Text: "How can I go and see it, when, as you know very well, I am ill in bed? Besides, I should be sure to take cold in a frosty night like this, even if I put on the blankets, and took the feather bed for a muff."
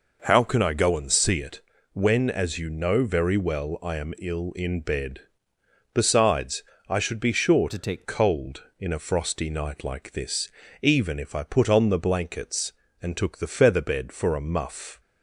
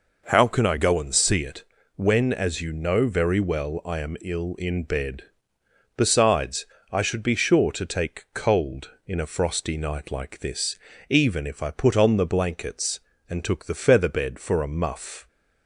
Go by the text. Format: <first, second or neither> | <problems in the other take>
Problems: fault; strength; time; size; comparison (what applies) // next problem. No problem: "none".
second | changes voice from "to" to "take"; from 7.6 to 8.0 s; 0.4 s long